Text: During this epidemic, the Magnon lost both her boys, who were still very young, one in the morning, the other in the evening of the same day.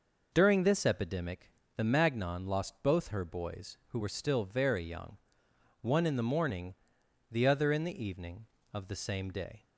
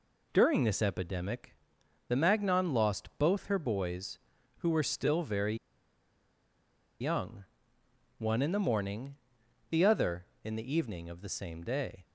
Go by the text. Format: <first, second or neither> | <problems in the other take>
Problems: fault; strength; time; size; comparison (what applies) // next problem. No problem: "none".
first | pauses between "very" and "young"; strong; at 5.5 s; 1.4 s long